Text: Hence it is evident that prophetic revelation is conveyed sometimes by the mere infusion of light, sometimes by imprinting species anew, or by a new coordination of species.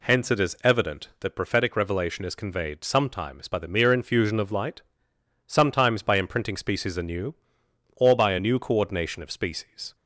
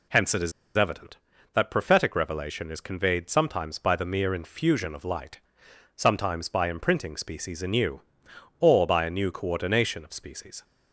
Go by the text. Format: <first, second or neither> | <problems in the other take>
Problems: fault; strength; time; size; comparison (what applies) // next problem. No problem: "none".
first | pauses between "is" and "evident"; slight; at 0.5 s; 0.25 s long